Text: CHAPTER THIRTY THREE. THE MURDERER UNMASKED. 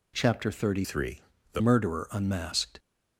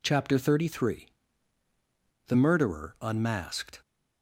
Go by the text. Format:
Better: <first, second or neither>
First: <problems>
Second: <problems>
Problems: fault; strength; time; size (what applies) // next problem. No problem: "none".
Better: second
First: changes voice from "THREE" to "THE"; from 0.8 to 1.6 s; 0.8 s long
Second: none